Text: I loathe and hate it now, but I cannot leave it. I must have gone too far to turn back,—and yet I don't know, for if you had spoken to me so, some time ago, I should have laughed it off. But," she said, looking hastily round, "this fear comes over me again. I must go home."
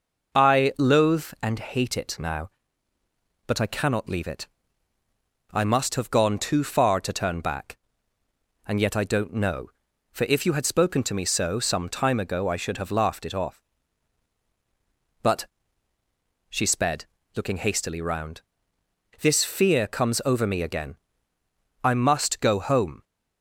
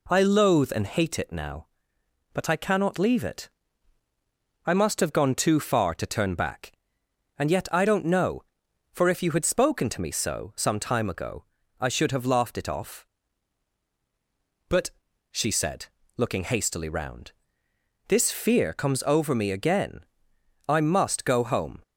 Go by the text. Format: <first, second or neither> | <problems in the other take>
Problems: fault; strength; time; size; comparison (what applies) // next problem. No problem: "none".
second | says "sped" for "said"; at 16.6 s